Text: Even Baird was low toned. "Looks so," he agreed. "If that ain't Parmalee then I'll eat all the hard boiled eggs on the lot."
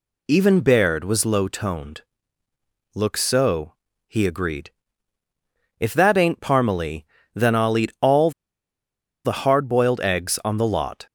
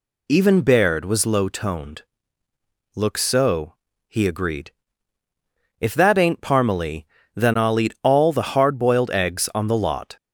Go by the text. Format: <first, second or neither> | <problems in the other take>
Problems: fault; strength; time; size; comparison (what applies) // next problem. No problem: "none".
second | pauses between "Parmalee" and "then"; slight; at 7.0 s; 0.30 s long; slight in the second // pauses between "all" and "the"; noticeable; at 8.3 s; 0.94 s long